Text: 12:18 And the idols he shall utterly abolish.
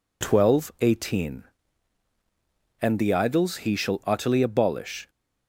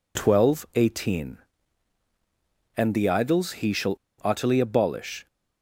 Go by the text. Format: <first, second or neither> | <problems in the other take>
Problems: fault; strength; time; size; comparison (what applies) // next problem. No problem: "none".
first | pauses between "shall" and "utterly"; slight; at 3.9 s; 0.25 s long